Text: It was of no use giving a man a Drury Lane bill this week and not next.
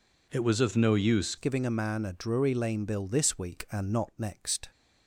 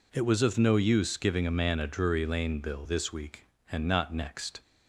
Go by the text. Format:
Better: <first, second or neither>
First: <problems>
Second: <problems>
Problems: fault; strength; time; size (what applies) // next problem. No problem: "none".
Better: second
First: changes voice at "giving"; from 1.3 s on; 3.4 s long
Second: none